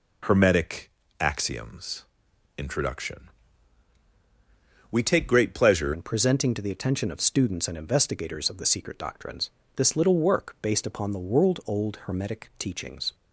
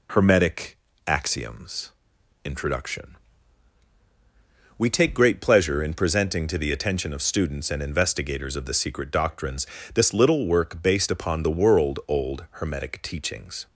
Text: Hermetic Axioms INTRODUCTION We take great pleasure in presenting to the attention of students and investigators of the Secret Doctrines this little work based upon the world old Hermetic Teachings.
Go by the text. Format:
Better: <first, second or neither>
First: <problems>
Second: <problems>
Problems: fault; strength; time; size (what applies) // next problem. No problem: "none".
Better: second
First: pauses between "Hermetic" and "Axioms"; slight; at 0.8 s; 0.30 s long // pauses between "Axioms" and "INTRODUCTION"; noticeable; at 2.0 s; 0.50 s long // pauses between "INTRODUCTION" and "We"; strong; at 3.2 s; 1.6 s long // changes voice at "in"; from 5.9 s on; 7.2 s long // pauses between "Doctrines" and "this"; slight; at 9.5 s; 0.24 s long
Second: pauses between "Hermetic" and "Axioms"; slight; at 0.7 s; 0.30 s long // pauses between "Axioms" and "INTRODUCTION"; noticeable; at 1.9 s; 0.50 s long // pauses between "INTRODUCTION" and "We"; strong; at 3.1 s; 1.6 s long // pauses between "Doctrines" and "this"; slight; at 9.6 s; 0.28 s long